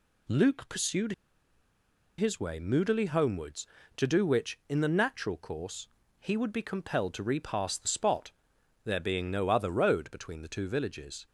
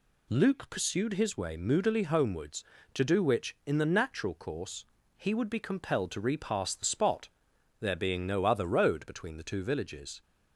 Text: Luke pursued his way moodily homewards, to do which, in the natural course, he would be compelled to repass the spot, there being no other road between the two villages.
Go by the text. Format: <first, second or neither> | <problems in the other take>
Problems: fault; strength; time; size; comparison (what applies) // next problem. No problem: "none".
second | pauses between "pursued" and "his"; at 1.1 s; 1.0 s long